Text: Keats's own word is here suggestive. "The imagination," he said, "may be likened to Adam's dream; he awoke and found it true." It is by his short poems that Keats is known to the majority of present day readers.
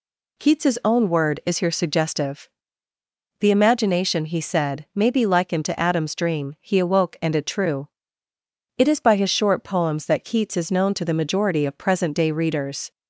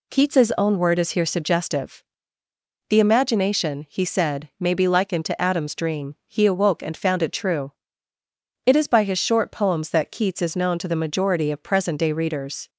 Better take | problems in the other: second | skips "found"; at 7.3 s

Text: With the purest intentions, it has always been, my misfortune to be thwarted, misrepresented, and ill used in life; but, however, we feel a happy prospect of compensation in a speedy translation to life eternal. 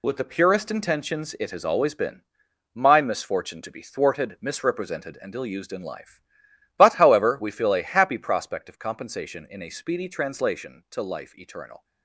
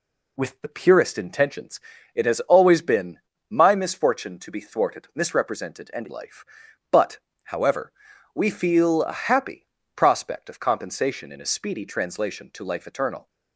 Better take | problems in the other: first | skips "ill used in"; at 6.0 s // pauses between "happy" and "prospect"; slight; at 9.6 s; 0.30 s long

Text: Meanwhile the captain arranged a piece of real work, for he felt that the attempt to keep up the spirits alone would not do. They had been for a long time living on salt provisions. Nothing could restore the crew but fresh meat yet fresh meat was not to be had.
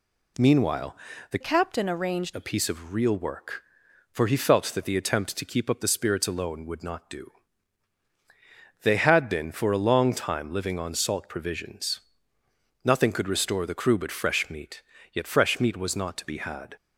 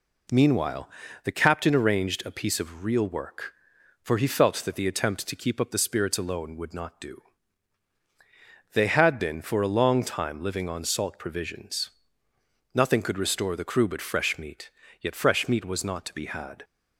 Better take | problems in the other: second | pauses between "Meanwhile" and "the"; slight; at 0.9 s; 0.36 s long; slight in the second // changes voice from "captain" to "arranged"; from 1.4 to 2.3 s; 0.9 s long // pauses between "meat" and "yet"; slight; at 14.8 s; 0.32 s long; slight in the second

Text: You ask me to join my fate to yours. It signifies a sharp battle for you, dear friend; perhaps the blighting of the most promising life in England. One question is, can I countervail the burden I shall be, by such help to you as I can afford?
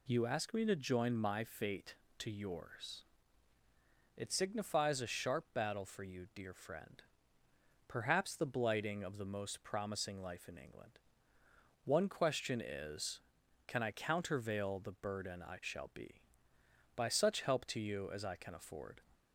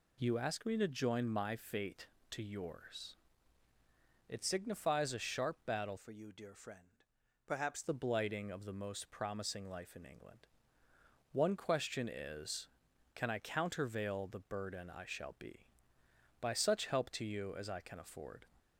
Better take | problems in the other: first | changes voice from "for" to "perhaps"; from 5.9 to 7.8 s; 1.9 s long

